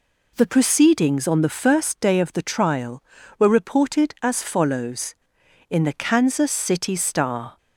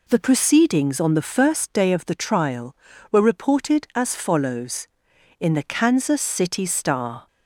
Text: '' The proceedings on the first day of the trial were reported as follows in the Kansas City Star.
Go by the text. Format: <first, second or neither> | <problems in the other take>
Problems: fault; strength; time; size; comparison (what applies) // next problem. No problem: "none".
neither | none